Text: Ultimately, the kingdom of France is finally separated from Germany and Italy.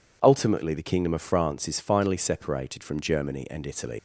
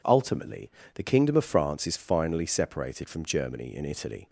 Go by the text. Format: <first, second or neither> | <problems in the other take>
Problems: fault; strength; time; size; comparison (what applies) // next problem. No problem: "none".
second | leaves "Italy" unfinished; at 3.9 s; 105 ms